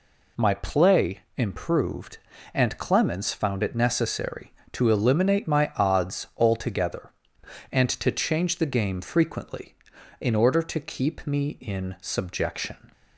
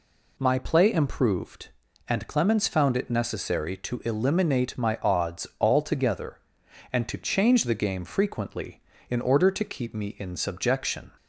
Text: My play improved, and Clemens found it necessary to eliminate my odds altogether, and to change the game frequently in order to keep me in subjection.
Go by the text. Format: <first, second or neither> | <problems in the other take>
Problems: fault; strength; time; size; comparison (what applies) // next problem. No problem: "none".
neither | none